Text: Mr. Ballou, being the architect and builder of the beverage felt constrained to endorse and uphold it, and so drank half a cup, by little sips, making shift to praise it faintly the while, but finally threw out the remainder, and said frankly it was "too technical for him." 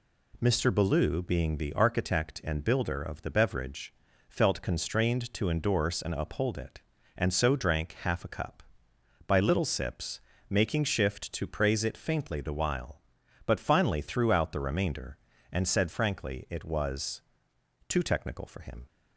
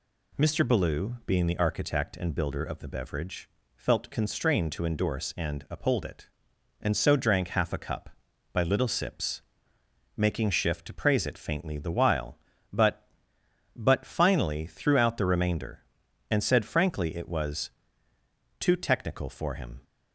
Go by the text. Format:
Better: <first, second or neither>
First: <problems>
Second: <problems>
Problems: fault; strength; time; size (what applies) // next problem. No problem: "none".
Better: first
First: pauses between "beverage" and "felt"; slight; at 3.9 s; 0.36 s long // pauses between "was" and "too"; noticeable; at 17.2 s; 0.66 s long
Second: pauses between "beverage" and "felt"; slight; at 3.4 s; 0.28 s long // says "but" twice; at 13.7 s // pauses between "was" and "too"; noticeable; at 17.6 s; 0.90 s long